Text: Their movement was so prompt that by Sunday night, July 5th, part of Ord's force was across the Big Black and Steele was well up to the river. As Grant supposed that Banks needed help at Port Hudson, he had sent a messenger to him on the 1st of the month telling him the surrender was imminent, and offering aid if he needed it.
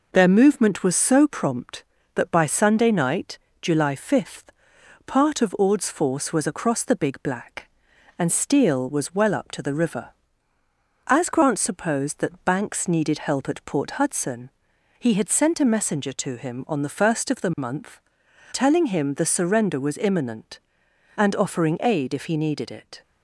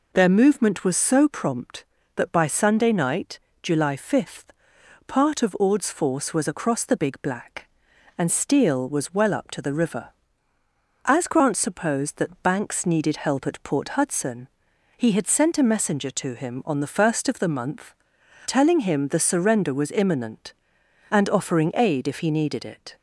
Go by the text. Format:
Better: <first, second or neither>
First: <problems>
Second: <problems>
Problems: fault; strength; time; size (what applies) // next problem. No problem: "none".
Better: second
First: gets quieter; slight; throughout; 2 dB // pauses between "month" and "telling"; noticeable; at 17.9 s; 0.54 s long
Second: pauses between "month" and "telling"; noticeable; at 17.9 s; 0.54 s long